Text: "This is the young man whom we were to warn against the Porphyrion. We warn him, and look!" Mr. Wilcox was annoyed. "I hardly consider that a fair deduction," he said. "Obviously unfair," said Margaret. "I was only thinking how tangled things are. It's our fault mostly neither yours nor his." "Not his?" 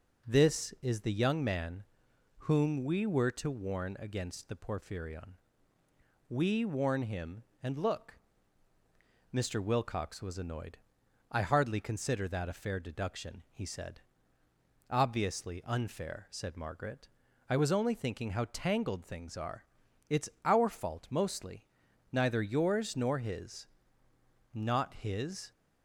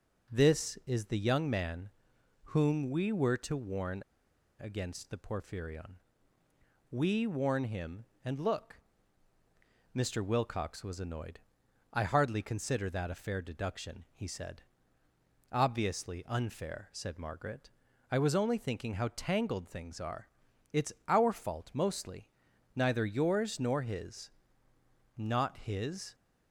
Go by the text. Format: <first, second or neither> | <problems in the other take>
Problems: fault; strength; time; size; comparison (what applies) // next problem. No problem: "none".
first | pauses between "man" and "whom"; noticeable; at 1.8 s; 0.64 s long; noticeable in the first // pauses between "warn" and "against"; noticeable; at 4.0 s; 0.57 s long // pauses between "It's" and "our"; slight; at 20.9 s; 0.16 s long; slight in the first // pauses between "mostly" and "neither"; noticeable; at 22.2 s; 0.46 s long; noticeable in the first